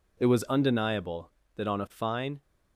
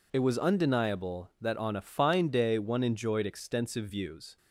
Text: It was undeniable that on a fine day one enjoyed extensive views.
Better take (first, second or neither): second